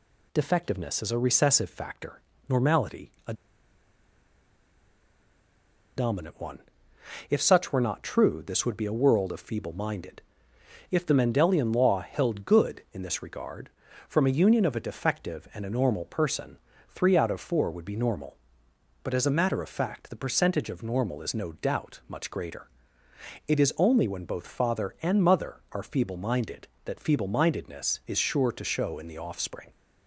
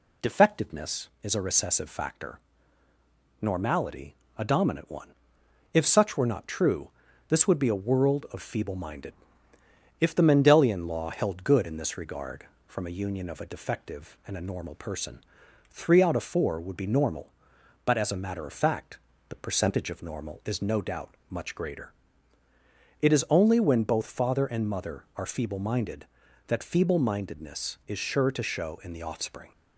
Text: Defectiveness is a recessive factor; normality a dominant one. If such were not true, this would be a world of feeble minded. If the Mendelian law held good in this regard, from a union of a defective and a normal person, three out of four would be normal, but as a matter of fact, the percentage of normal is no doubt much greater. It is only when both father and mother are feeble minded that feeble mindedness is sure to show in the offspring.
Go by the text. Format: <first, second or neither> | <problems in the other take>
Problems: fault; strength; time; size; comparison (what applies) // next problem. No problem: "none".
second | pauses between "normality" and "a"; slight; at 3.0 s; 0.16 s long; slight in the second // pauses between "a" and "dominant"; strong; at 3.3 s; 2.6 s long